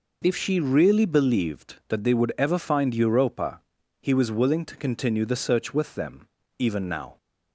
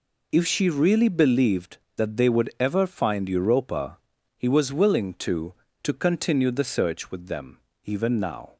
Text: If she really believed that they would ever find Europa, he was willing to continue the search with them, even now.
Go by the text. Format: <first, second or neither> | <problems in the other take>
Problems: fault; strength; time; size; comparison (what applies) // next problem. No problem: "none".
first | says "to" twice; at 5.8 s